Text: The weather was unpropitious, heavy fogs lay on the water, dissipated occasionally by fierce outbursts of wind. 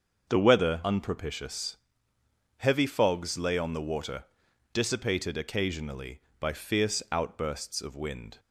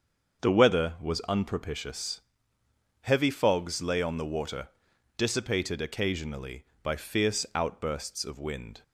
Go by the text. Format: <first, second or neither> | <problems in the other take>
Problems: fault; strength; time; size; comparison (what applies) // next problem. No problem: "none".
second | starts louder than the rest; until 1.3 s; 6.5 dB; also in the second // skips "was"; at 0.8 s